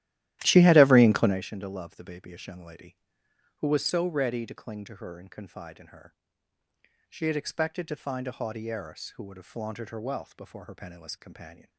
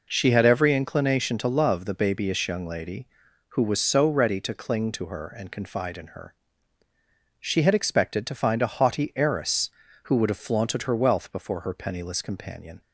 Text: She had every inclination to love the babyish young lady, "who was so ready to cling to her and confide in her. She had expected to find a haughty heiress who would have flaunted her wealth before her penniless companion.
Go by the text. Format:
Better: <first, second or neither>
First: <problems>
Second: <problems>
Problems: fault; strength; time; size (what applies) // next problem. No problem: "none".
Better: second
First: starts louder than the rest; strong; until 1.4 s; 14 dB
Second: none